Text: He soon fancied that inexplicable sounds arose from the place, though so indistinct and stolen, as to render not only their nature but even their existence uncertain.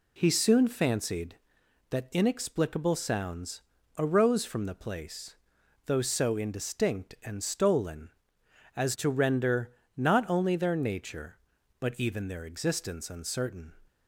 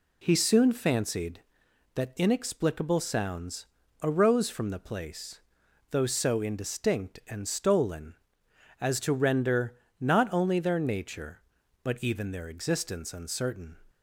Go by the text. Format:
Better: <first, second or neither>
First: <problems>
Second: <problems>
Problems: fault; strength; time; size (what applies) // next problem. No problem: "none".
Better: neither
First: pauses between "sounds" and "arose"; at 3.6 s; 0.38 s long // pauses between "render" and "not"; slight; at 9.6 s; 0.26 s long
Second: pauses between "sounds" and "arose"; at 3.6 s; 0.38 s long // pauses between "render" and "not"; slight; at 9.7 s; 0.26 s long